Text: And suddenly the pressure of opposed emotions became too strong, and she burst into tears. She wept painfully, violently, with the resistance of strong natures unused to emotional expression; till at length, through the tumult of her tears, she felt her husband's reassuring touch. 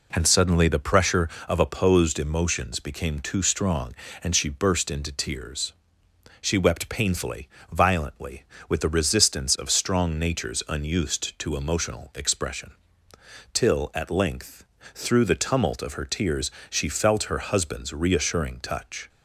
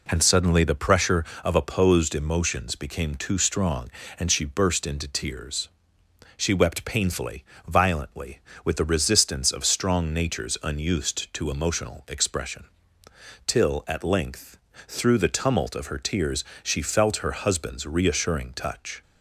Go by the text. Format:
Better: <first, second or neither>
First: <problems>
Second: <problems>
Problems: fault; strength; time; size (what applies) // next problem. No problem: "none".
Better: neither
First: none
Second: none